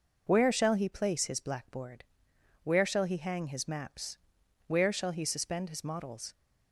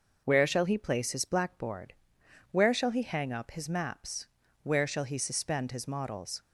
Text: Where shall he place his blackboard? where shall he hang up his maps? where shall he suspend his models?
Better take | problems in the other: second | skips "up"; at 3.4 s

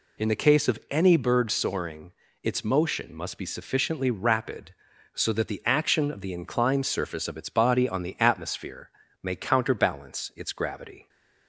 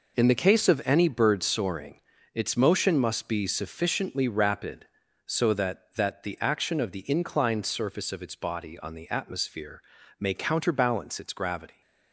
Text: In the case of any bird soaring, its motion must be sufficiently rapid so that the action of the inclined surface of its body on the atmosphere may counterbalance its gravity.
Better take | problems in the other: first | says "that" twice; at 5.9 s // pauses between "atmosphere" and "may"; at 9.8 s; 0.38 s long; slight in the first

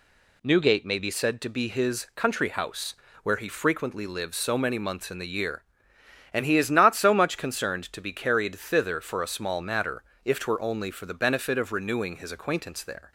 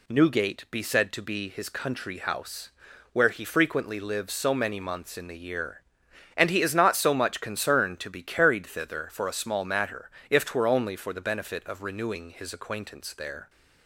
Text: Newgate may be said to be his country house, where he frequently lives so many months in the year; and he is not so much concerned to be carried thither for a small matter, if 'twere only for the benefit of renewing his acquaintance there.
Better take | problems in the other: first | skips "may"; at 0.6 s

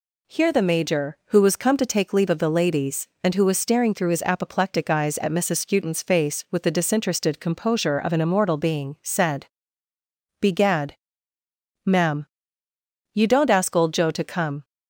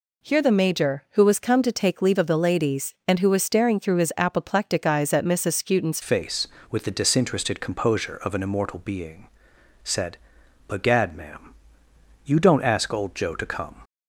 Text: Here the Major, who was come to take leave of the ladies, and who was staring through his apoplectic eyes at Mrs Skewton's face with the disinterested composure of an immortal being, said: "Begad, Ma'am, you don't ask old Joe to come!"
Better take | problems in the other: first | changes voice at "face"; from 6.0 s on; 7.8 s long

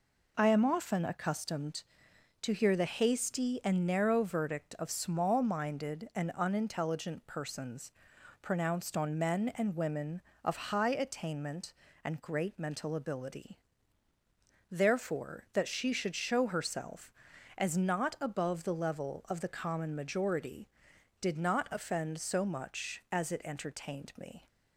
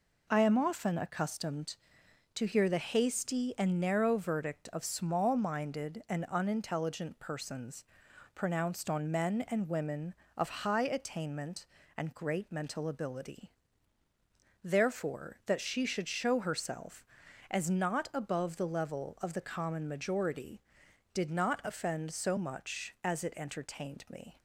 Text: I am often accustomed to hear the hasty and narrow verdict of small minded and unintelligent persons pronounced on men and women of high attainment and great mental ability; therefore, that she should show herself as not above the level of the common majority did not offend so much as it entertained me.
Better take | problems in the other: neither | pauses between "persons" and "pronounced"; noticeable; the same in both

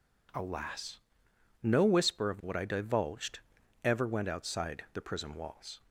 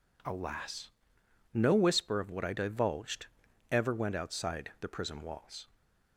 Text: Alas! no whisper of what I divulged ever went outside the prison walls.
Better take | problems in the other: neither | pauses between "divulged" and "ever"; the same in both

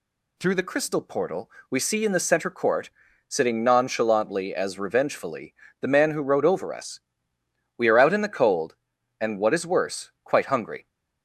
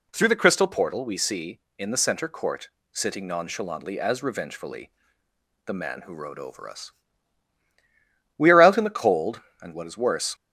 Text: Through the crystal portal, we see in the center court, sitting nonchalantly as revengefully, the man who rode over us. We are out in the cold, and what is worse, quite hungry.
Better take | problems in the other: first | stops before "quite hungry"; at 10.3 s

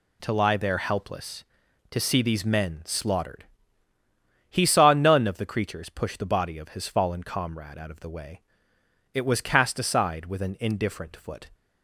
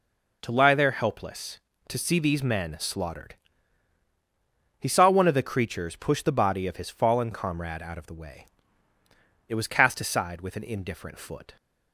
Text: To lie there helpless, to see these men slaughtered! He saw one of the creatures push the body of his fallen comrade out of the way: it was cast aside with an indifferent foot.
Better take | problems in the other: second | says "none" for "one"; at 4.9 s

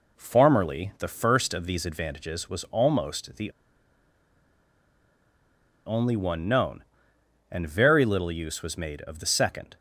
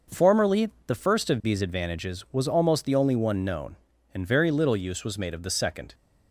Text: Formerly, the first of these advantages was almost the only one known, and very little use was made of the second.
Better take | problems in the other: second | pauses between "the" and "only"; strong; at 3.5 s; 2.3 s long

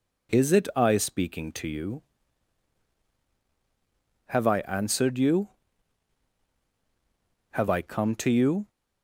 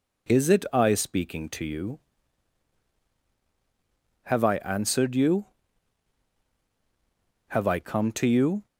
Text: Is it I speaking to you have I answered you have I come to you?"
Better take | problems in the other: neither | none

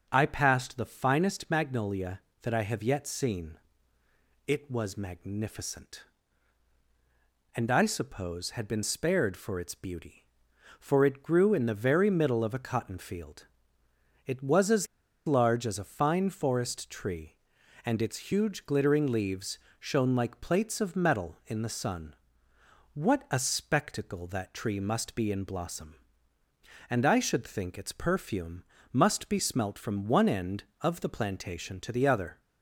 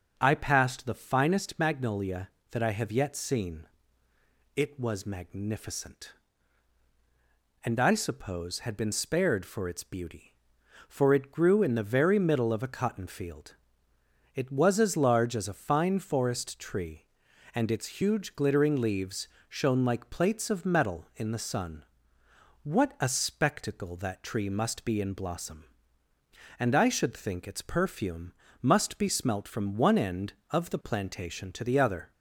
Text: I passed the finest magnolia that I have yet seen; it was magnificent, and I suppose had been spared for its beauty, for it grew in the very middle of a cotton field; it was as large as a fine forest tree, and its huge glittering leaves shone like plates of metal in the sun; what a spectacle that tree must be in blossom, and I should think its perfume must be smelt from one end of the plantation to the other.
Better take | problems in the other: second | starts louder than the rest; until 1.1 s; 6.5 dB; also in the second // pauses between "as" and "large"; at 14.8 s; 0.40 s long // pauses between "leaves" and "shone"; slight; at 19.5 s; 0.22 s long; slight in the second // pauses between "perfume" and "must"; slight; at 28.6 s; 0.30 s long; slight in the second

